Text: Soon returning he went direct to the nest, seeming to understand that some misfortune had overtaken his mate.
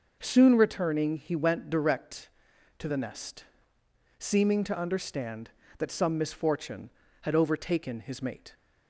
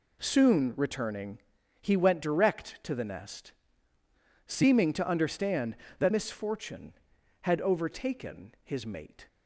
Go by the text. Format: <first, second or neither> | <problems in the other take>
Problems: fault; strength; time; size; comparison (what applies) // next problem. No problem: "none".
first | pauses between "returning" and "he"; at 1.3 s; 0.40 s long // skips "some"; at 6.1 s